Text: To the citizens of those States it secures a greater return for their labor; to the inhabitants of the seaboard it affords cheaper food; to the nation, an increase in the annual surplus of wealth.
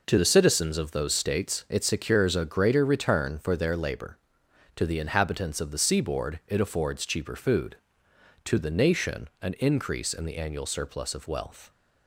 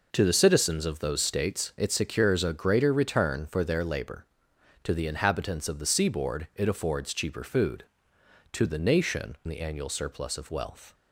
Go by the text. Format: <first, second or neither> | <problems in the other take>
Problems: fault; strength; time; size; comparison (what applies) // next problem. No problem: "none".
first | skips "an increase in"; at 9.4 s